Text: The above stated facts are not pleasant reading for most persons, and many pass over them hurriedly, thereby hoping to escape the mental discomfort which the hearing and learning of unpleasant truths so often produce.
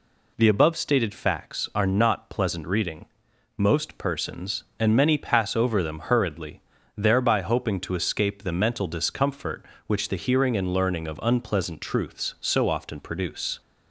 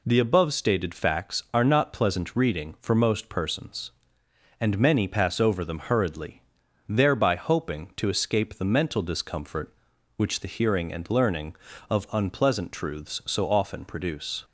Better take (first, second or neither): second